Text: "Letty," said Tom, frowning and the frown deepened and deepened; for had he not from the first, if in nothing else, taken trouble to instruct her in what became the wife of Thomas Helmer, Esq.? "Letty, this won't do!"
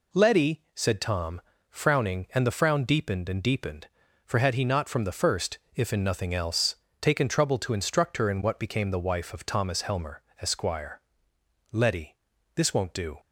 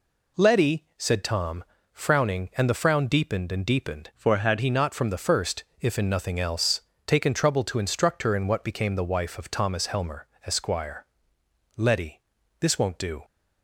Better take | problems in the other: first | changes voice from "for" to "had"; from 4.1 to 4.5 s; 0.4 s long

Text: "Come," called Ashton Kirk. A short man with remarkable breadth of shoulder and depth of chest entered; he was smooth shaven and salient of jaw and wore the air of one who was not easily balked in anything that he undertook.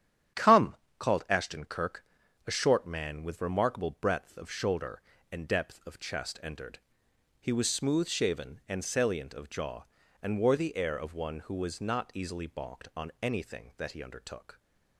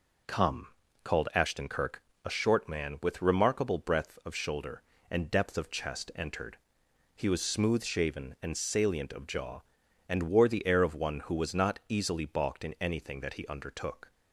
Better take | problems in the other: second | starts louder than the rest; strong; until 1.6 s; 9.5 dB // says "on" for "in"; at 12.9 s

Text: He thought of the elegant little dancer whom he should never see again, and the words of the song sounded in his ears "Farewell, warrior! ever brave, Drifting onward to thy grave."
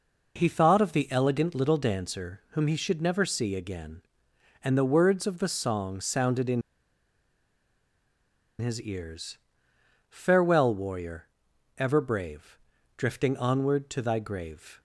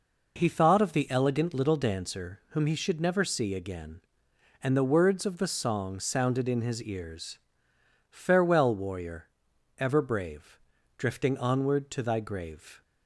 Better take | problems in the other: second | pauses between "in" and "his"; strong; at 6.6 s; 1.9 s long // pauses between "ears" and "Farewell"; noticeable; at 9.3 s; 0.72 s long; noticeable in the second

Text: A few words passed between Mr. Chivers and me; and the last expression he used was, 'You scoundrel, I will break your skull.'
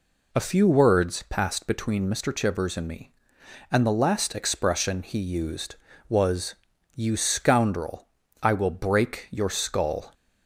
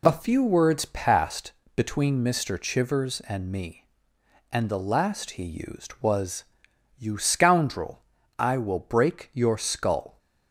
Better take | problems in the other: first | pauses between "passed" and "between"; slight; at 1.5 s; 0.24 s long // skips "expression"; at 5.4 s

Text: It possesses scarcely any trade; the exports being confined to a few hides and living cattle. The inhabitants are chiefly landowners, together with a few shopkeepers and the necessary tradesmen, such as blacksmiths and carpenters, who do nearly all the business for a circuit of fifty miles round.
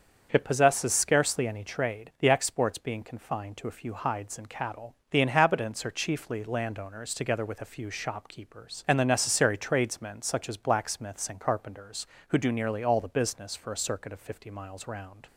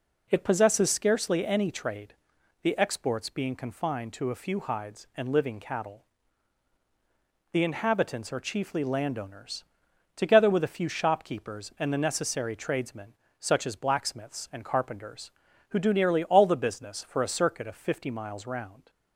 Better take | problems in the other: second | starts louder than the rest; until 1.3 s; 7 dB // skips "living"; at 4.4 s

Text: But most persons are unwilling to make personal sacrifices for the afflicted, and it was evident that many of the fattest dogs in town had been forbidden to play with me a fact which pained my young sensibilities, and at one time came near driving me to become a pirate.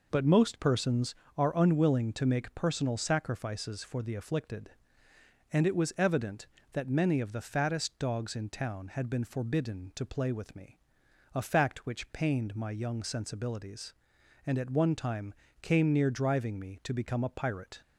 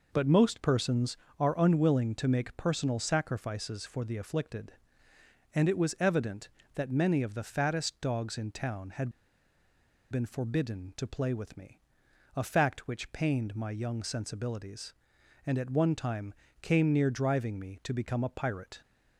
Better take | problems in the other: first | pauses between "had" and "been"; at 9.1 s; 1.0 s long // pauses between "me" and "a"; noticeable; at 11.7 s; 0.54 s long; noticeable in the first // pauses between "time" and "came"; slight; at 16.3 s; 0.30 s long; slight in the first

